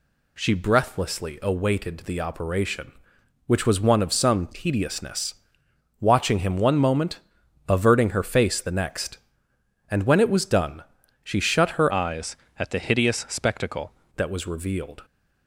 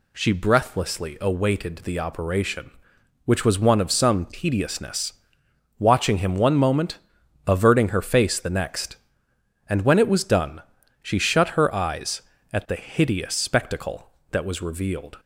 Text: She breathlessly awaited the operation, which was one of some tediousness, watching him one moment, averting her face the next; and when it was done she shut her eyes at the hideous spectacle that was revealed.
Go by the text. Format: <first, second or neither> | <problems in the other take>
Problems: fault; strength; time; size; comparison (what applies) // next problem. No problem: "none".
second | pauses between "done" and "she"; at 10.8 s; 0.40 s long; also in the second // changes voice from "eyes" to "spectacle"; from 11.9 to 13.9 s; 2.0 s long